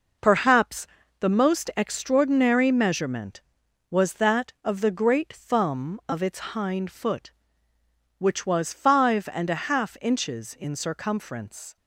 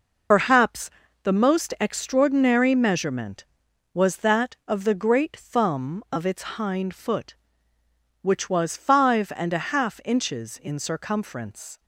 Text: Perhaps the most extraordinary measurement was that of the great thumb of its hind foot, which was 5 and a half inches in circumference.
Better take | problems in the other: first | loses the start of "Perhaps"; at 0.3 s; 65 ms // pauses between "Perhaps" and "the"; slight; at 0.9 s; 0.32 s long; slight in the first

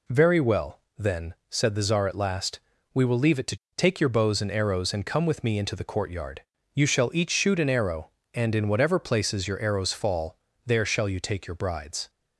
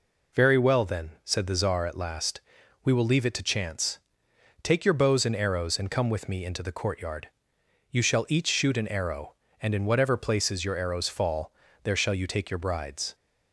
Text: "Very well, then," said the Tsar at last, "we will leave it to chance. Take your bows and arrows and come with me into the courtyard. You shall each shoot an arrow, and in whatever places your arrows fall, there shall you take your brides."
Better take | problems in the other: second | skips "chance"; at 3.6 s

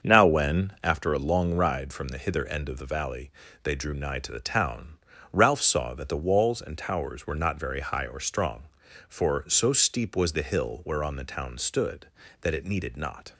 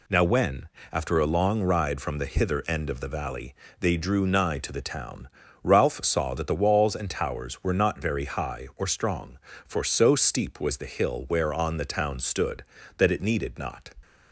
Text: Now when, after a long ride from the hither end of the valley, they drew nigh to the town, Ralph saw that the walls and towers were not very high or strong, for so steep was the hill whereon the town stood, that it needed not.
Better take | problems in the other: second | starts louder than the rest; until 1.0 s; 6.5 dB

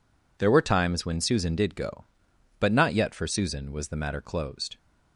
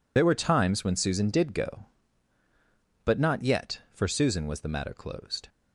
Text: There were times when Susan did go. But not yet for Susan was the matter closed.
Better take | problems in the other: first | loses the start of "There"; at 0.1 s; 65 ms

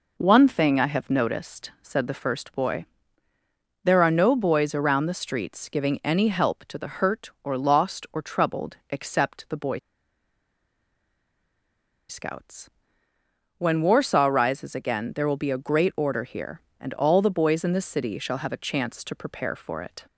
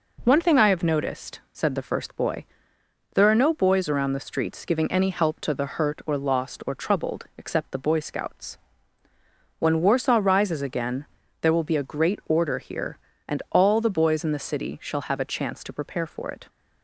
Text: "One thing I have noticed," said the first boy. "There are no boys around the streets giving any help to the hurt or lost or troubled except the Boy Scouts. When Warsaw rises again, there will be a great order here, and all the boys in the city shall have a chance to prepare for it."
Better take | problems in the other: second | pauses between "Boy" and "Scouts"; strong; at 9.7 s; 2.3 s long

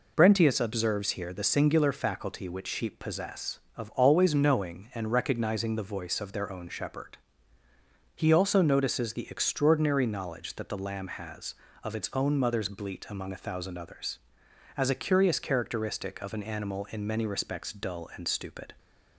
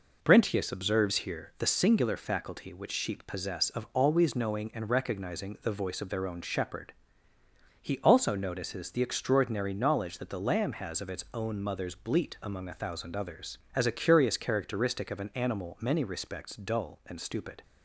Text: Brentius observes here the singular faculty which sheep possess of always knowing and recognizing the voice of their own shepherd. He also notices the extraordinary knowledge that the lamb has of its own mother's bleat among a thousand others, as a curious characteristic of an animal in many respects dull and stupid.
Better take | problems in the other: first | skips "in"; at 15.7 s

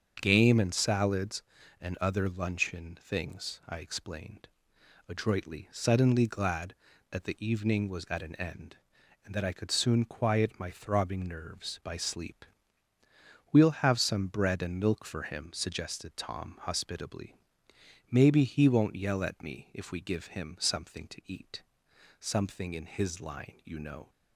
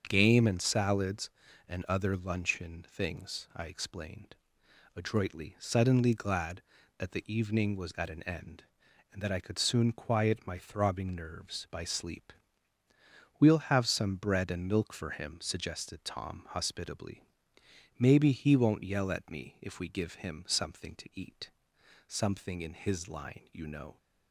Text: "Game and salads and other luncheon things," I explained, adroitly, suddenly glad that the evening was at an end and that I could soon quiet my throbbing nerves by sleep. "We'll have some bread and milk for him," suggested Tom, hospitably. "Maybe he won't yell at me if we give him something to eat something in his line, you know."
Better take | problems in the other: neither | starts louder than the rest; the same in both // pauses between "eat" and "something"; noticeable; the same in both

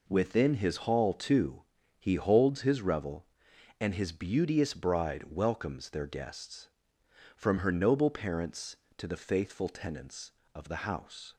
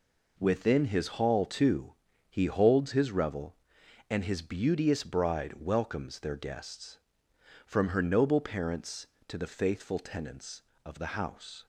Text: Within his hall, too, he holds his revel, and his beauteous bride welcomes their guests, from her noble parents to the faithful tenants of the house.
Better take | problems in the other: neither | none

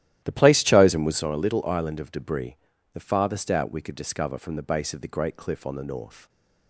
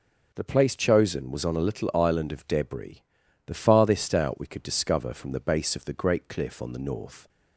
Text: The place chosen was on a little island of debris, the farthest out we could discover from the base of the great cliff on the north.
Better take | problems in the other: second | starts louder than the rest; strong; until 1.3 s; 13.5 dB

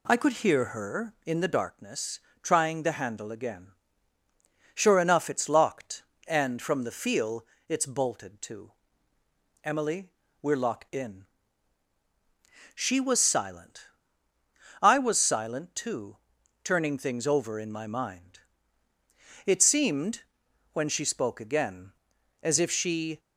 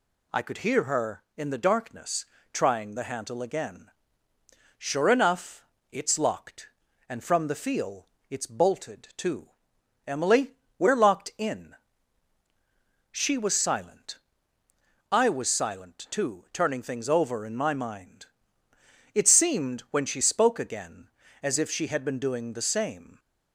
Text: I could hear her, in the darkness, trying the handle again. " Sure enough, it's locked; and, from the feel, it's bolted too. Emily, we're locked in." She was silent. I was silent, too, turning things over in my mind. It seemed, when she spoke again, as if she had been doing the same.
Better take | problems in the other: second | stops before "had been doing the same"; at 23.1 s

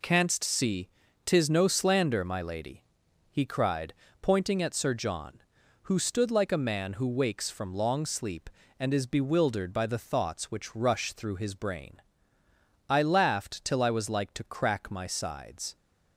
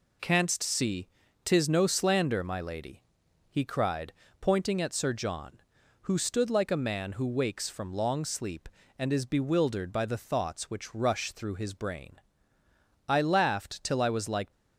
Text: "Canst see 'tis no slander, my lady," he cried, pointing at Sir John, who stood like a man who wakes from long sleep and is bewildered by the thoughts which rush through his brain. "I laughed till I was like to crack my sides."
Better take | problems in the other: first | pauses between "see" and "tis"; at 1.0 s; 0.38 s long; also in the first // stops before "to crack my sides"; at 14.5 s

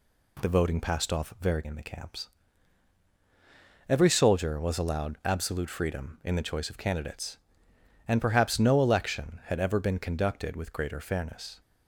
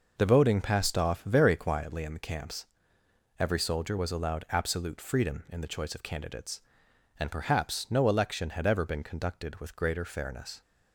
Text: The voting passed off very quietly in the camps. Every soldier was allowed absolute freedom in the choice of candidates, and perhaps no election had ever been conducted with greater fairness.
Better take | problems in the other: second | skips "quietly"; at 1.6 s

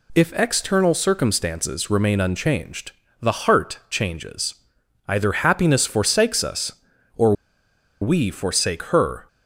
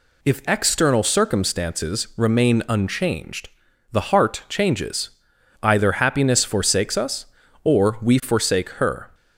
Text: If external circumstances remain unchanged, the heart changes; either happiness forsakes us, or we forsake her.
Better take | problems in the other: second | pauses between "or" and "we"; noticeable; at 7.3 s; 0.68 s long

